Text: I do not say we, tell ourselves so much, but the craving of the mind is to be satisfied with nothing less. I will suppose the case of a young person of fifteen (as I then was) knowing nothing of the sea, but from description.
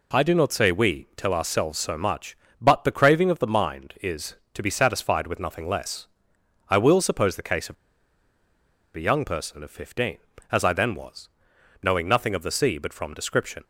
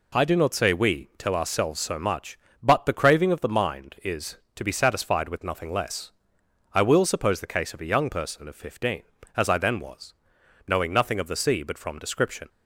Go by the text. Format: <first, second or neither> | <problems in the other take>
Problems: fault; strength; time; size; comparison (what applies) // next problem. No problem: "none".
second | pauses between "of" and "a"; at 7.7 s; 1.2 s long